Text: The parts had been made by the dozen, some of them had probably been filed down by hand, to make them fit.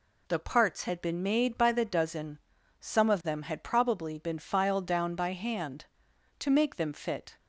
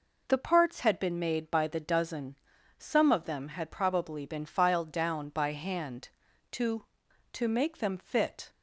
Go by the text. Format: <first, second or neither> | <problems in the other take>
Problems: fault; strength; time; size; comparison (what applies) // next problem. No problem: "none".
first | says "to" twice; at 7.3 s